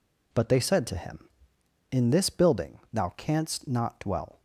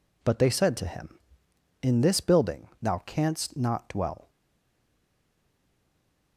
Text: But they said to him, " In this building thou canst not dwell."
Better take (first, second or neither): first